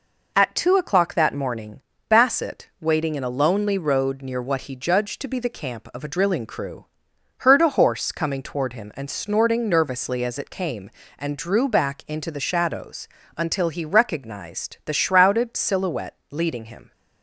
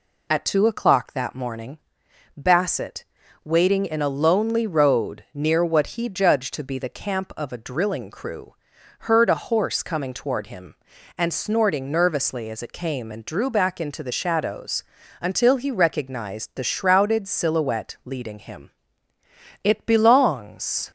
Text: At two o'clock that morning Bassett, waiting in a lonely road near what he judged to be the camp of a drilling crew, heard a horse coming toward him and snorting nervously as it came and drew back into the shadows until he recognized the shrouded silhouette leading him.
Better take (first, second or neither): first